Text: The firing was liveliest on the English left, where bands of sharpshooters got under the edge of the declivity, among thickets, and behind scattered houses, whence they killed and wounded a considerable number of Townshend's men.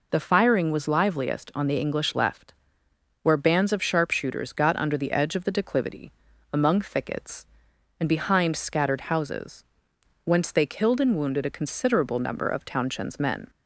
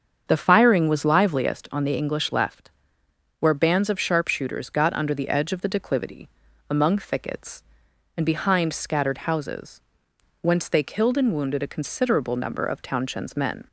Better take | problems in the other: first | starts louder than the rest; strong; until 1.7 s; 7 dB

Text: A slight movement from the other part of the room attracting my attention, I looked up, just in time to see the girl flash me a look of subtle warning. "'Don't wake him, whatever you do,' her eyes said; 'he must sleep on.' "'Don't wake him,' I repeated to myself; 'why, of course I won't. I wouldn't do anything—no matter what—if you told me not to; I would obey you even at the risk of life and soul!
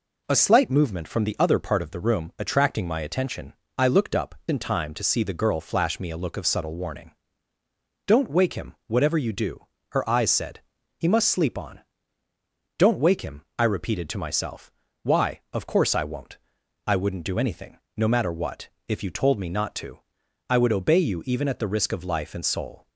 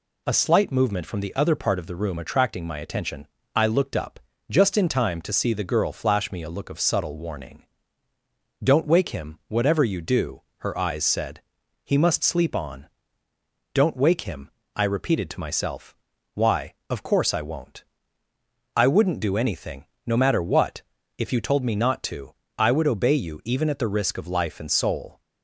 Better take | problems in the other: second | skips "just"; at 4.4 s

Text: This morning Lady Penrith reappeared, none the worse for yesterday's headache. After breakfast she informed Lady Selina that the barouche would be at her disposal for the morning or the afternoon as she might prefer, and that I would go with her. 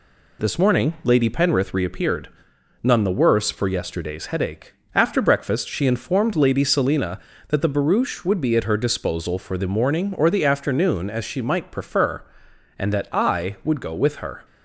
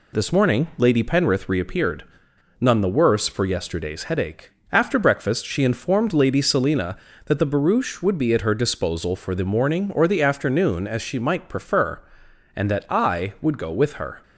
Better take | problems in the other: neither | none

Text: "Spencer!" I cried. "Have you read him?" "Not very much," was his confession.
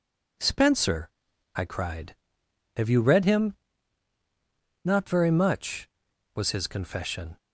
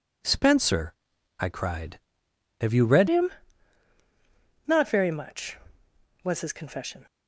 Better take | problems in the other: first | changes voice at "him"; from 3.0 s on; 4.0 s long

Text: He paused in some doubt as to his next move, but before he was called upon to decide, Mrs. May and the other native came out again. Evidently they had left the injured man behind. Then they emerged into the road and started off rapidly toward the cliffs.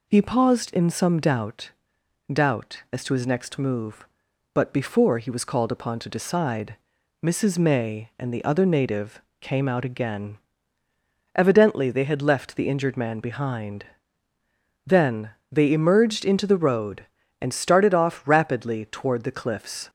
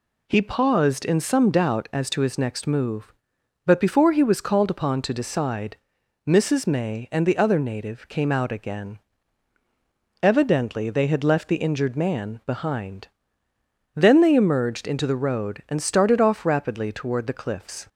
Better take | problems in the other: second | says "doubt" twice; at 2.3 s // pauses between "native" and "came"; slight; at 9.2 s; 0.18 s long // pauses between "Then" and "they"; slight; at 15.2 s; 0.20 s long

